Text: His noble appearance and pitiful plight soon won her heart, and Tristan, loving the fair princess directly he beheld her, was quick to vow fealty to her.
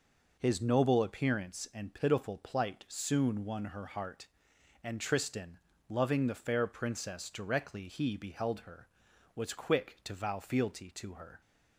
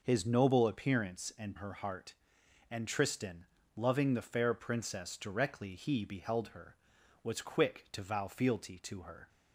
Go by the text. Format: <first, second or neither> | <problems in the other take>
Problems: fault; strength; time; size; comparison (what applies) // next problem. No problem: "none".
first | skips "pitiful plight soon won"; at 1.5 s